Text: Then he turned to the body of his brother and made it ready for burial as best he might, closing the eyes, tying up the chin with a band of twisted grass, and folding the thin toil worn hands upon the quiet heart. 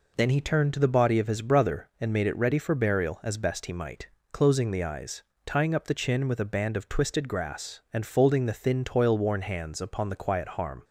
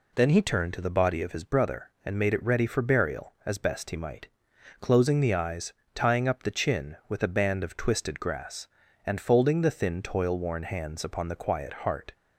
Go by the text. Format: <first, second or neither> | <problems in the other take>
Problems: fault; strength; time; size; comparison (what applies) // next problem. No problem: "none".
second | says "harm" for "heart"; at 10.4 s